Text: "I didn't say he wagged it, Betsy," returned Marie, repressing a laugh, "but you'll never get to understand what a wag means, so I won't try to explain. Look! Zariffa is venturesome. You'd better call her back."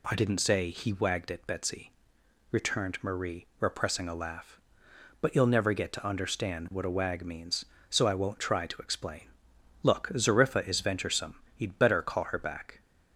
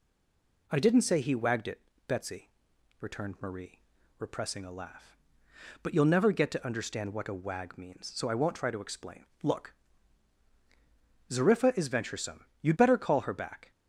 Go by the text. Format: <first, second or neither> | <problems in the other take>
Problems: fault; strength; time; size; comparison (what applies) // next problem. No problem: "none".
first | stays silent before the first word; slight; until 0.6 s; 0.6 s long